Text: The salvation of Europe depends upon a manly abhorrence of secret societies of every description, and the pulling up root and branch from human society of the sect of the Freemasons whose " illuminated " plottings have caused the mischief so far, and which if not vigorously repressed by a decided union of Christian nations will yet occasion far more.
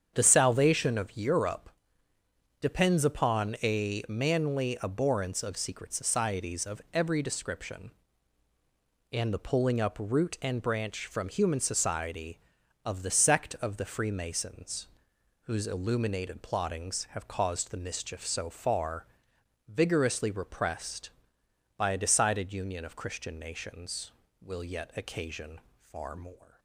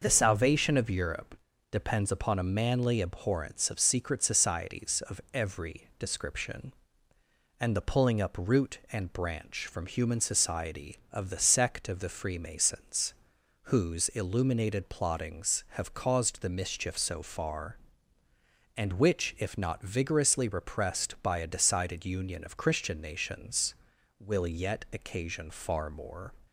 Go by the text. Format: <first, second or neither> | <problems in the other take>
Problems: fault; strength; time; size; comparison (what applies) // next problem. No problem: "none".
second | starts louder than the rest; strong; until 1.1 s; 8 dB // pauses between "Europe" and "depends"; noticeable; at 1.6 s; 0.92 s long; slight in the second // pauses between "Freemasons" and "whose"; noticeable; at 14.8 s; 0.60 s long; noticeable in the second // skips "and which if not"; at 19.3 s // pauses between "occasion" and "far"; slight; at 25.5 s; 0.32 s long